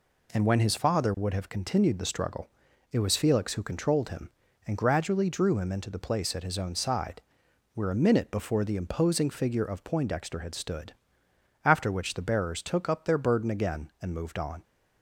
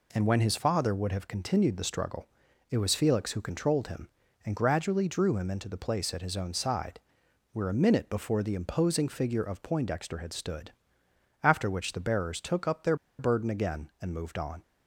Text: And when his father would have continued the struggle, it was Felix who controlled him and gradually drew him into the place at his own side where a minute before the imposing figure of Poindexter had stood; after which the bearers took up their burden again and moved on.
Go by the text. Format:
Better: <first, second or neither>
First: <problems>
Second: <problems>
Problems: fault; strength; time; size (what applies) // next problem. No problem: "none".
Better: first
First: pauses between "side" and "where"; noticeable; at 7.2 s; 0.54 s long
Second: pauses between "side" and "where"; noticeable; at 6.9 s; 0.54 s long // pauses between "their" and "burden"; slight; at 12.9 s; 0.23 s long